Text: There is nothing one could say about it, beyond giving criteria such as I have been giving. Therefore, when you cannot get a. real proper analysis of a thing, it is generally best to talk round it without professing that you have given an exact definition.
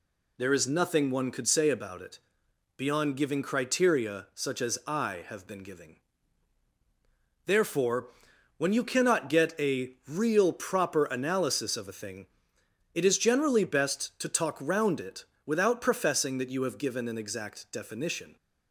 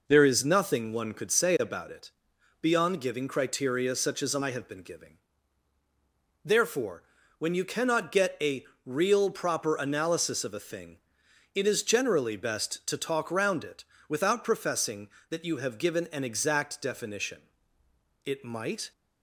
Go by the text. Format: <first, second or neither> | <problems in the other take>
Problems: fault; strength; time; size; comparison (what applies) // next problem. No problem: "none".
first | pauses between "it" and "without"; slight; at 13.8 s; 0.24 s long; slight in the first // goes on to say "It might"; noticeable; from 18.2 s on; 0.68 s long